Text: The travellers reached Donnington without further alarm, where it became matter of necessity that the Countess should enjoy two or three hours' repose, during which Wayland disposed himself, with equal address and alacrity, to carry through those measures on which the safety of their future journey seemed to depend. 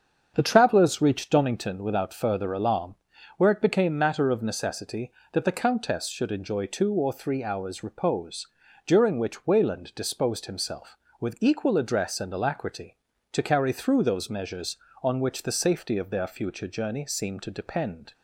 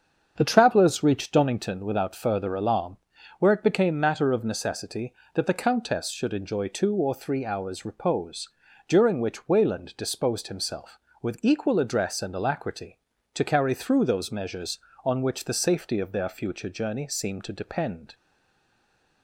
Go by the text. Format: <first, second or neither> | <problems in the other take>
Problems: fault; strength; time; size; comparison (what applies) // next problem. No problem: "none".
first | starts louder than the rest; strong; until 1.3 s; 7 dB; strong in the first // stays silent after the last word; from 18.1 s on; 1.1 s long